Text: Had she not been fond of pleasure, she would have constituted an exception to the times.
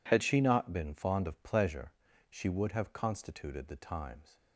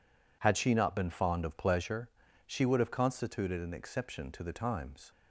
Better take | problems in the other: second | skips "an exception to"; at 3.6 s

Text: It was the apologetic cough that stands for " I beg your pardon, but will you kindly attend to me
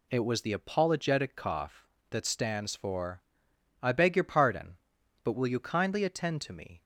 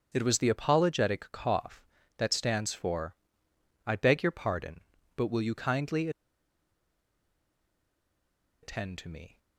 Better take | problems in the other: first | pauses between "kindly" and "attend"; strong; at 6.0 s; 2.5 s long

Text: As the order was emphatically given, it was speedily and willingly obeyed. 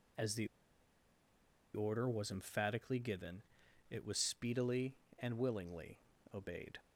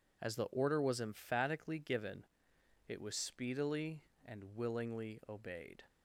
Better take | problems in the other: second | pauses between "the" and "order"; strong; at 0.4 s; 1.2 s long // pauses between "willingly" and "obeyed"; slight; at 5.9 s; 0.36 s long

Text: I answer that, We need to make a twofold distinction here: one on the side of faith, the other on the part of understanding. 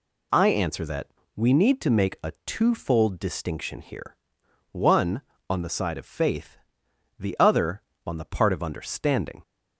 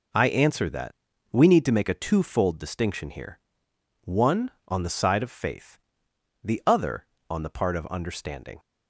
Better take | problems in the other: neither | none

